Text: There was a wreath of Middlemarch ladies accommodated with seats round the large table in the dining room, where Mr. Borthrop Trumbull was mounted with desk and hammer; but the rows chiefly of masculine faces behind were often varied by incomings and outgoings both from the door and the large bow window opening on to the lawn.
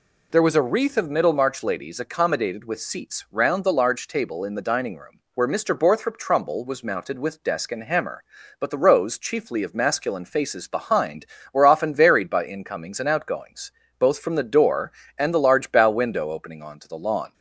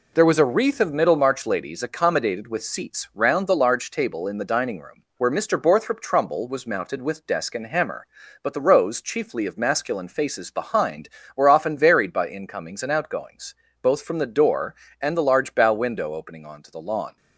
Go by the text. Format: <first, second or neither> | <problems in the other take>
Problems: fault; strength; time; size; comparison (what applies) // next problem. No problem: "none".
first | gets quieter; noticeable; throughout; 6 dB // pauses between "outgoings" and "both"; slight; at 13.5 s; 0.26 s long; slight in the first